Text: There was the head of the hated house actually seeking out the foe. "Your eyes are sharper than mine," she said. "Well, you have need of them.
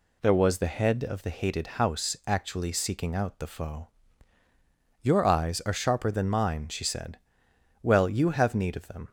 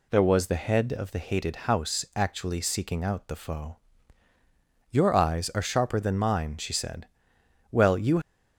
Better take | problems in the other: first | stops before "have need of them"; at 8.2 s

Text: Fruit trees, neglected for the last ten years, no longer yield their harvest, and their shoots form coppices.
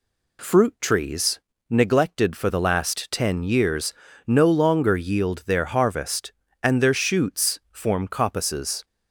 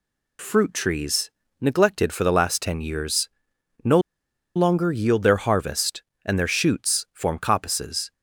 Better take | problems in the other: first | pauses between "no" and "longer"; noticeable; at 4.0 s; 0.55 s long

